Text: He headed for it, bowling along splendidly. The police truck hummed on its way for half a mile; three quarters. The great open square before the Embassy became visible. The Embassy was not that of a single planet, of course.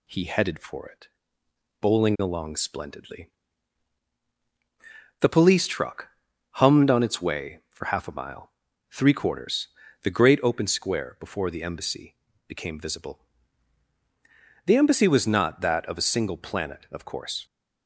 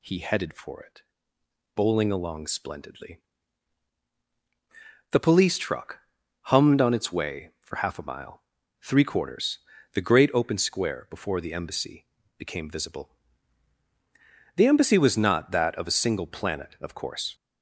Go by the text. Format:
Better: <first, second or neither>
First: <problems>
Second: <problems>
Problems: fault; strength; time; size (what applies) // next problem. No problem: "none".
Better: first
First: pauses between "truck" and "hummed"; at 6.0 s; 0.42 s long // pauses between "Embassy" and "became"; slight; at 12.1 s; 0.34 s long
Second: gets louder; throughout; 4 dB // pauses between "truck" and "hummed"; at 6.0 s; 0.42 s long // pauses between "Embassy" and "became"; slight; at 12.0 s; 0.34 s long